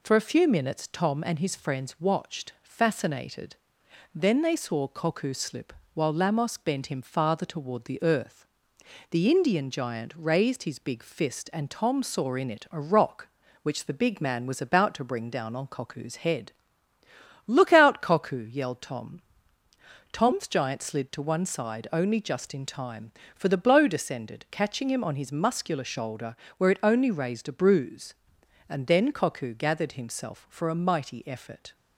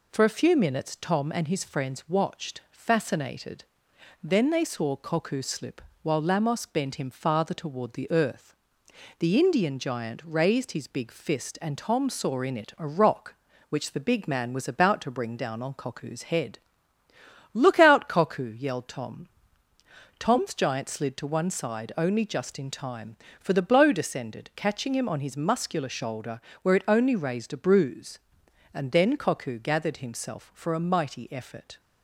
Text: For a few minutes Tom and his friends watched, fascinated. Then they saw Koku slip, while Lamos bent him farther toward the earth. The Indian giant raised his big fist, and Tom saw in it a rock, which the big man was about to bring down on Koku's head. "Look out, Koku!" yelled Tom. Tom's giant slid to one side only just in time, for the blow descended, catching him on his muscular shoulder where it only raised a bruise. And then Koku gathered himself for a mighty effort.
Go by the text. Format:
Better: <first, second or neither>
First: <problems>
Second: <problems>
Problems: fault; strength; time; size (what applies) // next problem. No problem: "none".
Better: neither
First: pauses between "shoulder" and "where"; slight; at 26.3 s; 0.22 s long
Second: pauses between "shoulder" and "where"; slight; at 26.4 s; 0.22 s long